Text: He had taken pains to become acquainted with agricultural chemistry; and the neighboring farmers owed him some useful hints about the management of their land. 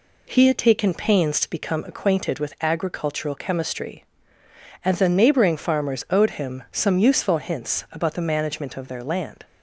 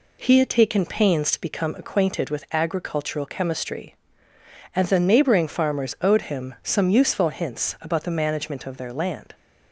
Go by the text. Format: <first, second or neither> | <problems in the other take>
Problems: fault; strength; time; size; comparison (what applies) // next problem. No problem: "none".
neither | none